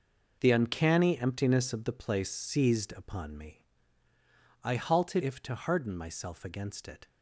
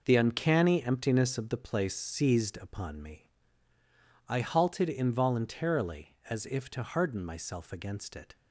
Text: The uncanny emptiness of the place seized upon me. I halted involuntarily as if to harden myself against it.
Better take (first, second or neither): second